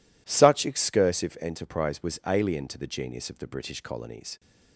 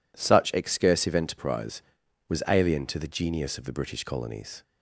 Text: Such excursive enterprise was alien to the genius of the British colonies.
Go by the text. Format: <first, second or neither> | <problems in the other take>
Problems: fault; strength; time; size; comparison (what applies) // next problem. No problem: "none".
neither | none